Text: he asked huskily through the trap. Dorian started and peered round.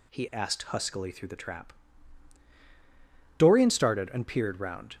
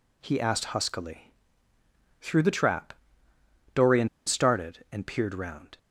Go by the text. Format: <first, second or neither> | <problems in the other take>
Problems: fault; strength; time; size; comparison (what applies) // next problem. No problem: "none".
first | pauses between "huskily" and "through"; noticeable; at 1.3 s; 0.90 s long // pauses between "Dorian" and "started"; slight; at 4.0 s; 0.19 s long